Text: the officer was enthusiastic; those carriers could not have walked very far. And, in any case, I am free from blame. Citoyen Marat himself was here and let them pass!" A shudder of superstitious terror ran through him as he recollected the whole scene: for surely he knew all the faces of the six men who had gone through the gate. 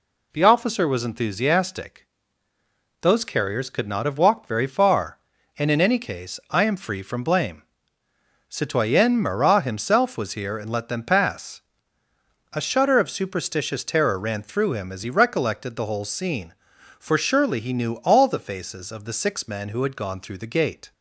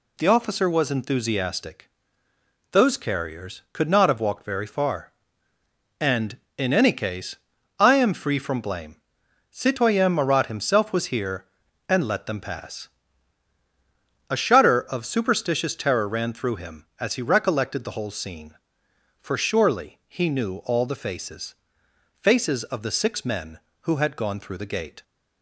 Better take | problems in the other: first | says "faces" twice; at 22.2 s

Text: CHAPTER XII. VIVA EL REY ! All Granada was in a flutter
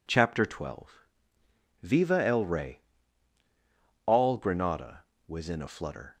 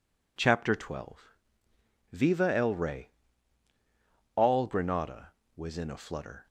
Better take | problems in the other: neither | none

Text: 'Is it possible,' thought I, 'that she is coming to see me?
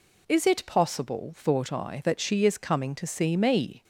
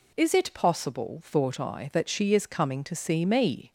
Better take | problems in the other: neither | none

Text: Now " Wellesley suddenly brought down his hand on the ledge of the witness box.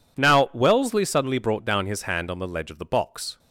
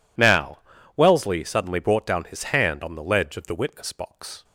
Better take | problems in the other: second | skips "witness"; at 2.8 s

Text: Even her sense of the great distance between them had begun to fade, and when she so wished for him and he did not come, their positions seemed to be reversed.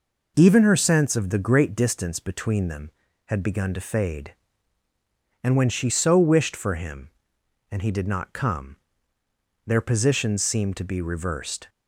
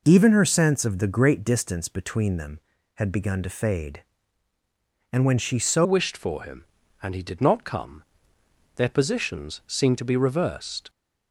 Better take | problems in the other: first | changes voice at "wished"; from 5.8 s on; 5.0 s long

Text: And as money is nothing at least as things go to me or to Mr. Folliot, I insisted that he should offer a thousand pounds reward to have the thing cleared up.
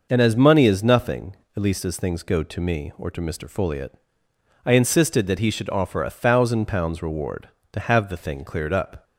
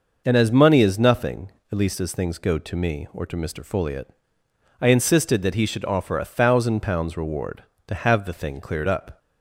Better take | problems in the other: neither | none

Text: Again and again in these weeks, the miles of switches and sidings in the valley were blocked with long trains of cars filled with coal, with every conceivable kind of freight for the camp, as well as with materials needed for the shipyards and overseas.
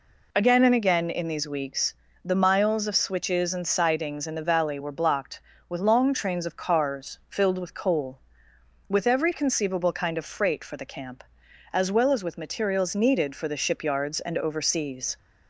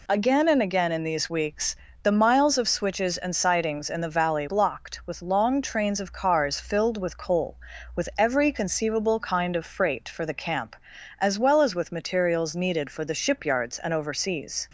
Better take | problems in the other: first | skips "were"; at 4.4 s

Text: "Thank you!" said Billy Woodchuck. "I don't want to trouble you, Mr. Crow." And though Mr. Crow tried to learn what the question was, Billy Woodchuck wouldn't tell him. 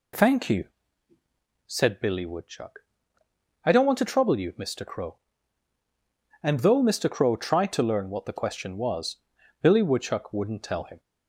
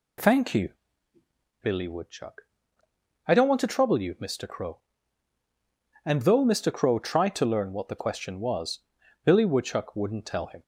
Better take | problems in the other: first | skips "said"; at 1.1 s

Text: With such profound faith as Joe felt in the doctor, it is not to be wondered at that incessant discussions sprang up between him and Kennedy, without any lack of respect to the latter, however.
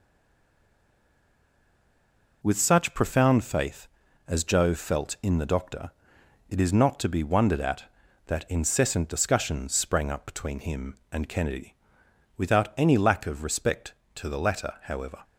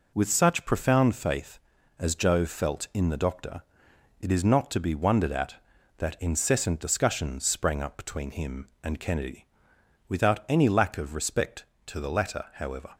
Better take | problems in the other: second | stays silent before the first word; until 2.4 s; 2.4 s long

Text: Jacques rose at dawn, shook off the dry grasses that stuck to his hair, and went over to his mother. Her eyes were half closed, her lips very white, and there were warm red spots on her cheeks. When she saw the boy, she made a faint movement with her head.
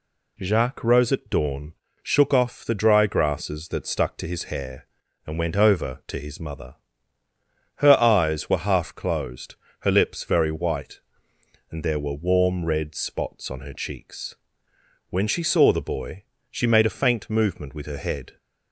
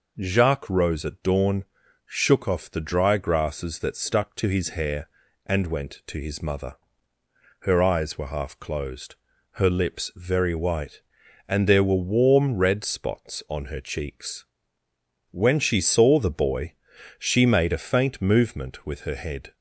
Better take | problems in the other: first | skips "over"; at 6.0 s

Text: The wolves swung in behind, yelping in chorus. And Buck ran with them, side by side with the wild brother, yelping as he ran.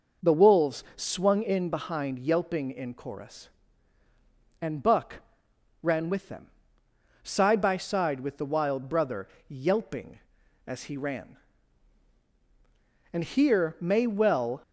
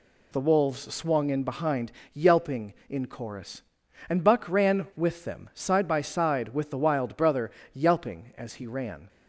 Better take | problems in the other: second | pauses between "Buck" and "ran"; noticeable; at 5.1 s; 0.66 s long // goes on to say "And here may well"; from 13.1 s on; 1.5 s long

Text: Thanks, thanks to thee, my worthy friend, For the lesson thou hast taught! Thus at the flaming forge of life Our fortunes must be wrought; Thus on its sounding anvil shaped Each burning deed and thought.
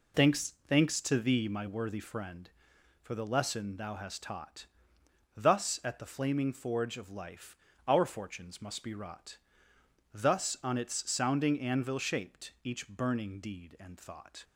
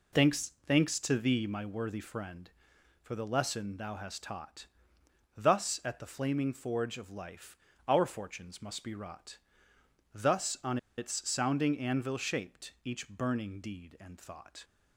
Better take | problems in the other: first | pauses between "life" and "Our"; slight; at 7.5 s; 0.30 s long; slight in the first // pauses between "on" and "its"; slight; at 10.7 s; 0.19 s long

